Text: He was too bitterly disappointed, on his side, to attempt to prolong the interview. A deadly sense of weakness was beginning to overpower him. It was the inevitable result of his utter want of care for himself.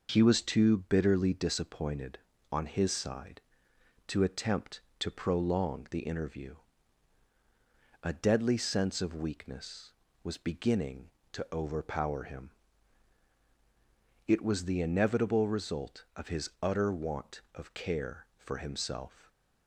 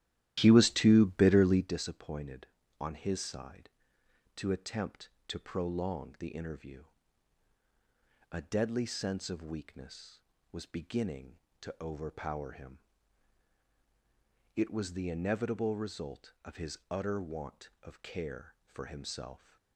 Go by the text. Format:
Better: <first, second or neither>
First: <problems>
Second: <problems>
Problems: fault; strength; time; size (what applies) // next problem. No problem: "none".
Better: first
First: none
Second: starts louder than the rest; strong; until 1.8 s; 13.5 dB